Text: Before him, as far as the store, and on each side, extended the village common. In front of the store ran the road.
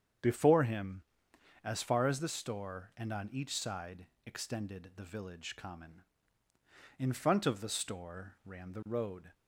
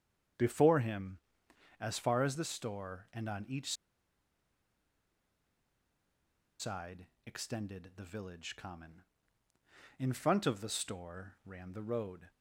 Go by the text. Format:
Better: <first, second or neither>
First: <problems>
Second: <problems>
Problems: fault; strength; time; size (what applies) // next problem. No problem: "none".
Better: first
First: starts louder than the rest; strong; until 1.8 s; 8 dB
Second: starts louder than the rest; strong; until 2.0 s; 8 dB // pauses between "each" and "side"; strong; at 3.7 s; 2.8 s long